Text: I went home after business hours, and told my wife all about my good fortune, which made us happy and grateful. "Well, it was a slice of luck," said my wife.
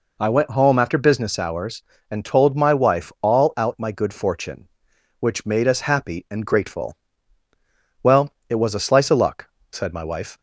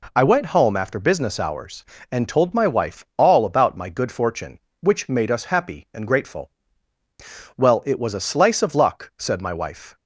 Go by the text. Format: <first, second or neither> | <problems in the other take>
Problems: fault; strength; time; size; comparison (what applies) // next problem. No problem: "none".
second | says "out" for "about"; at 3.5 s